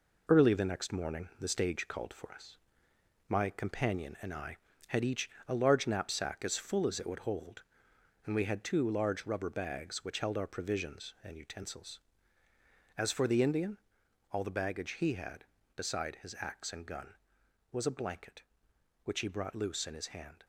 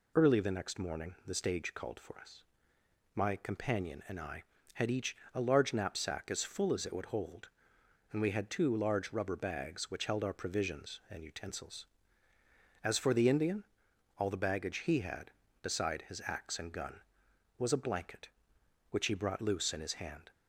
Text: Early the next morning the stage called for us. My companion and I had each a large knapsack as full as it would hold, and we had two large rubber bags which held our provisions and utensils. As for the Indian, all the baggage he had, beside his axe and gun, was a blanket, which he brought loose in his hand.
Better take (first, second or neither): second